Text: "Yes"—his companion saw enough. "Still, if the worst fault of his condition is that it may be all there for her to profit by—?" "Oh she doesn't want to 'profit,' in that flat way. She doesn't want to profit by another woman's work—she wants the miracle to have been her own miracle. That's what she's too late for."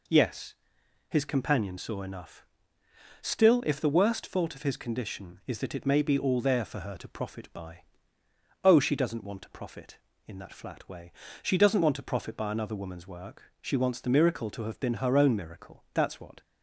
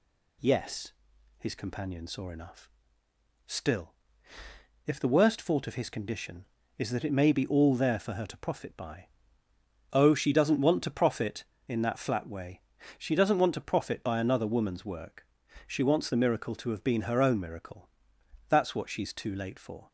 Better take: second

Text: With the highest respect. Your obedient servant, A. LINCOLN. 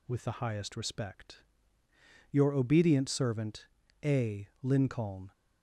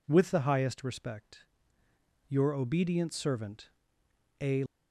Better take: first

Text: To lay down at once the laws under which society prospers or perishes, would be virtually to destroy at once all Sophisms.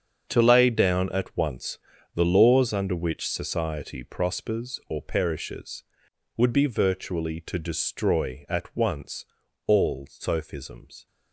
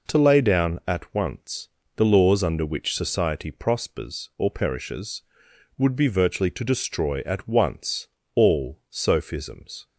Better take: second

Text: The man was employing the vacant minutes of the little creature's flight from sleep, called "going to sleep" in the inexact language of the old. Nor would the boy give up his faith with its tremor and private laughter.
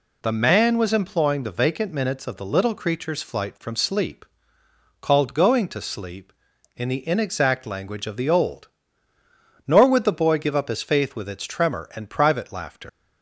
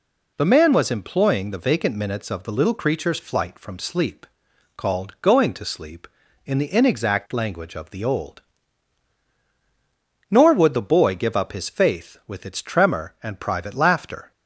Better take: second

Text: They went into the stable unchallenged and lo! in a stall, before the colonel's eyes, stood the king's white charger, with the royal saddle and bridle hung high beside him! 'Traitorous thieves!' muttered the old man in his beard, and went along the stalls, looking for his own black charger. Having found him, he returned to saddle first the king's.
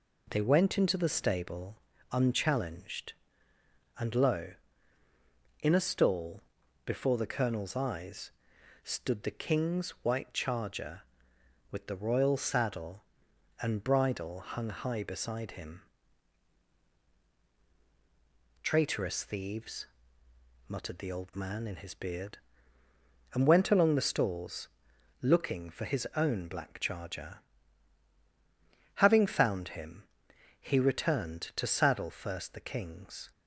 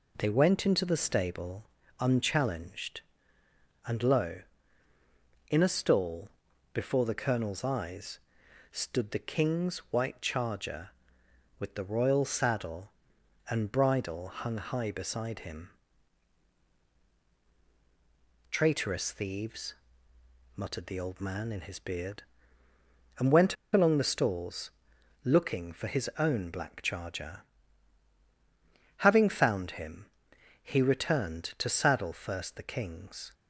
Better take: first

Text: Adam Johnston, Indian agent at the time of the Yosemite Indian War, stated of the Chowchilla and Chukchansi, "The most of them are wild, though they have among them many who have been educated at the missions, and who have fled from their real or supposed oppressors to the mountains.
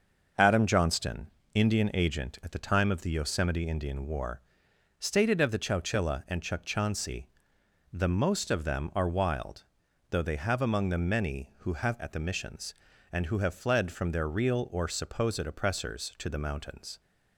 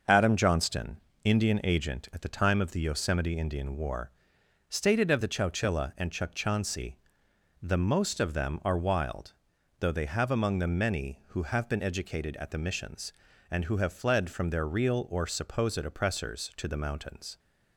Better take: second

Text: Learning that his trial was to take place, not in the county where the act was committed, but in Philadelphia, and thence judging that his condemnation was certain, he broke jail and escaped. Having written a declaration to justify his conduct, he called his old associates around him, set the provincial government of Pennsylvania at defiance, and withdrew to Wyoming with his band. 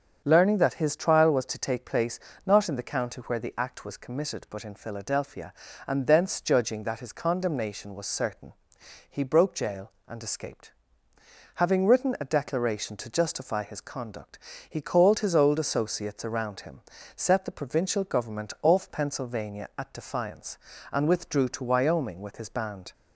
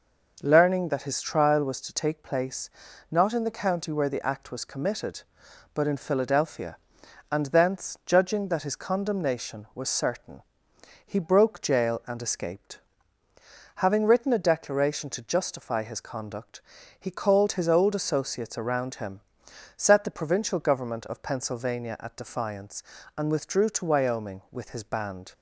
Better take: second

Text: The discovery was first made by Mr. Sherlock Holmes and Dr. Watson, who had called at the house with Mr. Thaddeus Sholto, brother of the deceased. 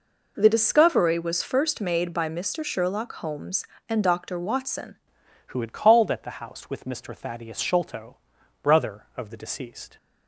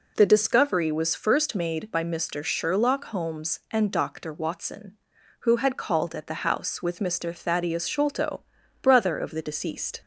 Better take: second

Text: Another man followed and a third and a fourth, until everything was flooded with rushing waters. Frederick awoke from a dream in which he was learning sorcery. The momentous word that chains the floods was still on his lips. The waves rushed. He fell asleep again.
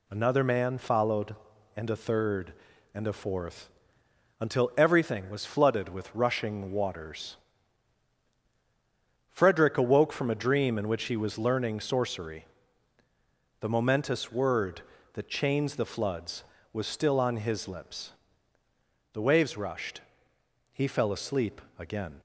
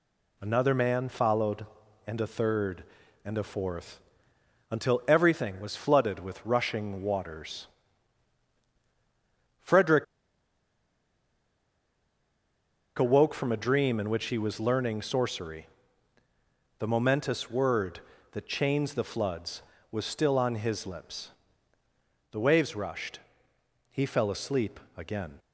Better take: first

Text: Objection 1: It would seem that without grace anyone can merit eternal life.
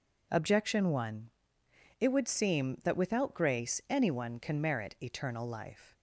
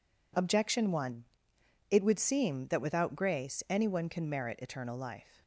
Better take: neither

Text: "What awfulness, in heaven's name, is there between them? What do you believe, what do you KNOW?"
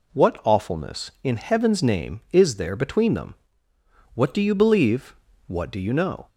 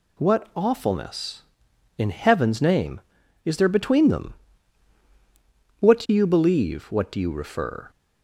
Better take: first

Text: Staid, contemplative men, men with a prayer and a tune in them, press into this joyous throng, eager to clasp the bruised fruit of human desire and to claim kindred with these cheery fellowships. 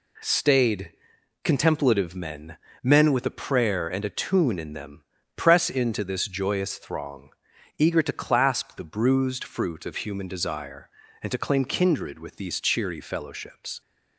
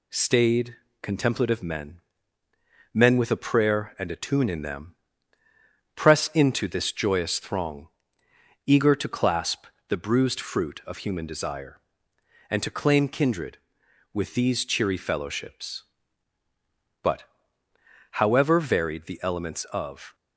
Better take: first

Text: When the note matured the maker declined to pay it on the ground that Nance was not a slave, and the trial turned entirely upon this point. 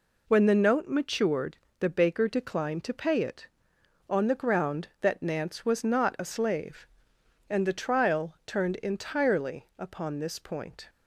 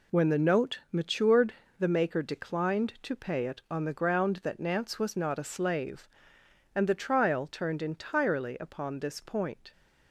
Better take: second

